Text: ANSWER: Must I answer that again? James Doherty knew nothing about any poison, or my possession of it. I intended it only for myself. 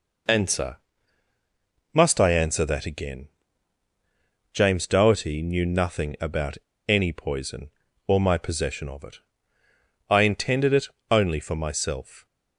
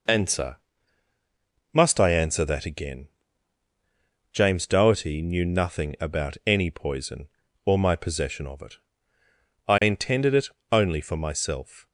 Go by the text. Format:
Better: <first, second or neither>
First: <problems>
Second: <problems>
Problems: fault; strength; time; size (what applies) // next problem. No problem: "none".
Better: second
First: pauses between "about" and "any"; slight; at 6.5 s; 0.29 s long // pauses between "it" and "only"; slight; at 10.8 s; 0.24 s long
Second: pauses between "it" and "only"; slight; at 10.4 s; 0.24 s long